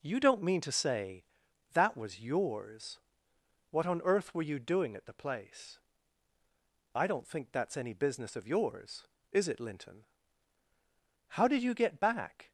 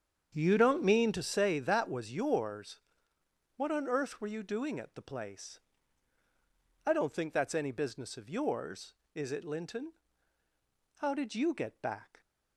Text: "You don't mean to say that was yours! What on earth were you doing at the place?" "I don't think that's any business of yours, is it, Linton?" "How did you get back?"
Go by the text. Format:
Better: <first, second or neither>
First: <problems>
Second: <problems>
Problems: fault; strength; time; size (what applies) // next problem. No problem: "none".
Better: first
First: none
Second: starts louder than the rest; strong; until 1.5 s; 7.5 dB